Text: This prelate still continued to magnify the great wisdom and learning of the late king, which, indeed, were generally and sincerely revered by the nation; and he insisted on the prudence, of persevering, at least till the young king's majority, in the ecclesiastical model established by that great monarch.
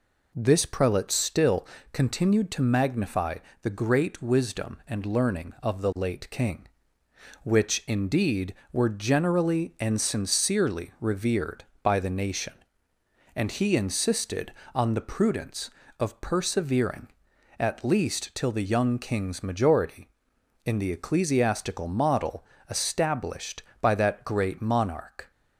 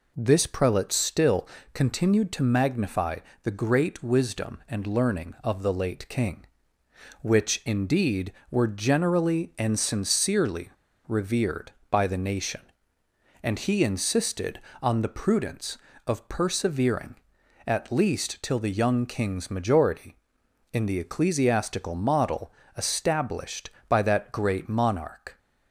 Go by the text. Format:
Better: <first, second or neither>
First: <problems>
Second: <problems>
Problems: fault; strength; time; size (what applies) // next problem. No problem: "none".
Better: first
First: pauses between "still" and "continued"; slight; at 1.6 s; 0.26 s long // pauses between "magnify" and "the"; slight; at 3.3 s; 0.24 s long // pauses between "model" and "established"; slight; at 22.4 s; 0.24 s long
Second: pauses between "still" and "continued"; slight; at 1.4 s; 0.26 s long // pauses between "magnify" and "the"; slight; at 3.1 s; 0.24 s long // pauses between "sincerely" and "revered"; at 10.7 s; 0.37 s long // pauses between "model" and "established"; slight; at 22.5 s; 0.24 s long